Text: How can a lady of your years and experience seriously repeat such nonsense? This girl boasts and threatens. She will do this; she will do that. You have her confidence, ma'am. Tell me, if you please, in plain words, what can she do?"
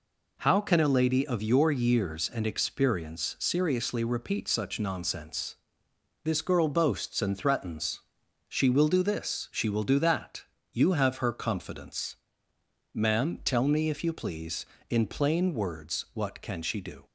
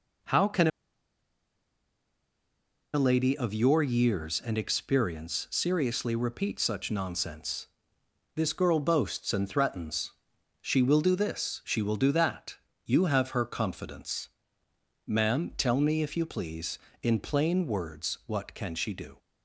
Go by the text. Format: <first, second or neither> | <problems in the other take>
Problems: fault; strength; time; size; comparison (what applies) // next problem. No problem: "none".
first | pauses between "can" and "a"; strong; at 0.6 s; 2.2 s long